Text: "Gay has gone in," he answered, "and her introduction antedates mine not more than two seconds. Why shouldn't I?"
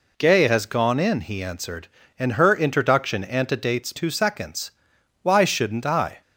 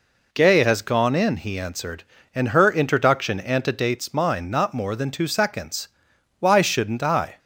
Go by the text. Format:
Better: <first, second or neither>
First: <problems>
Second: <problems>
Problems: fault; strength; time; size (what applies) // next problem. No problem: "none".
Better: second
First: skips "mine not more than"; at 3.9 s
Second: none